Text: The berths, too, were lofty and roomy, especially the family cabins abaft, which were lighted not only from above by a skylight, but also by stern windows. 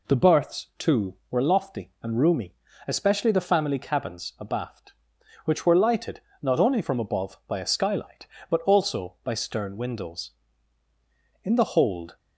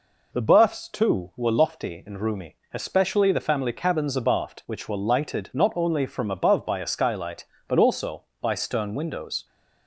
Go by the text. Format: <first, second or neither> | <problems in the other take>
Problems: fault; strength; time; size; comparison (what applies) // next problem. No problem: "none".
second | pauses between "lighted" and "not"; slight; at 6.2 s; 0.22 s long // goes on to say "In the hold"; noticeable; from 11.4 s on; 0.74 s long